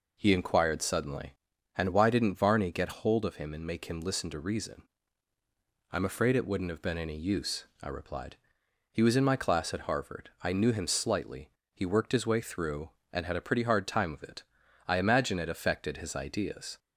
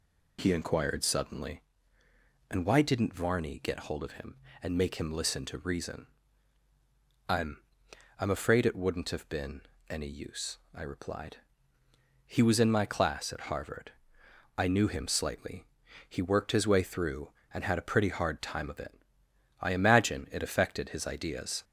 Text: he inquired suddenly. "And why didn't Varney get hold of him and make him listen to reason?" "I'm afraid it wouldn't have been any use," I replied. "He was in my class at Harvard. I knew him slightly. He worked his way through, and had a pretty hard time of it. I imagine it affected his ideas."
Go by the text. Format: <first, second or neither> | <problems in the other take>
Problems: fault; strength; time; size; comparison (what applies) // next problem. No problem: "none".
first | says "I'm" twice; at 8.2 s // pauses between "been" and "any"; slight; at 9.6 s; 0.28 s long